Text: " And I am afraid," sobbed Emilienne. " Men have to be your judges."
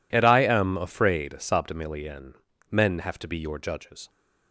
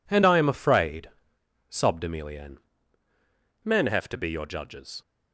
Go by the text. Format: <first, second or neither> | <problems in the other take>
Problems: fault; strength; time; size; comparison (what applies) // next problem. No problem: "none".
neither | none